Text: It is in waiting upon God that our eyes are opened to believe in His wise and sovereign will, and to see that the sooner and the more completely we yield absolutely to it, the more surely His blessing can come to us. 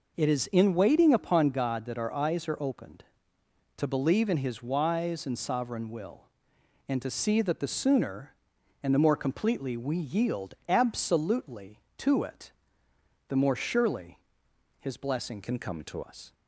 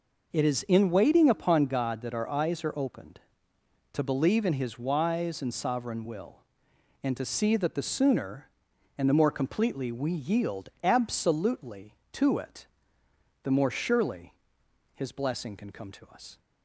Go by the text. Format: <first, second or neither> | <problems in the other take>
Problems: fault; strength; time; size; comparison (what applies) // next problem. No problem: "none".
second | pauses between "surely" and "His"; noticeable; at 14.1 s; 0.60 s long; noticeable in the second // changes voice from "can" to "to"; from 15.4 to 16.0 s; 0.6 s long